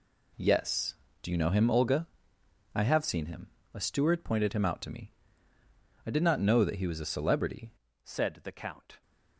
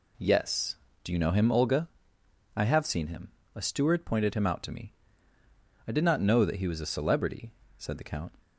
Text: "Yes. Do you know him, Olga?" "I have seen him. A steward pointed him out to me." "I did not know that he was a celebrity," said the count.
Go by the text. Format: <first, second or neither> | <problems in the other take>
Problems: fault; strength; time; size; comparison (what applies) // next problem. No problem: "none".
second | changes voice at "said"; from 8.0 s on; 1.0 s long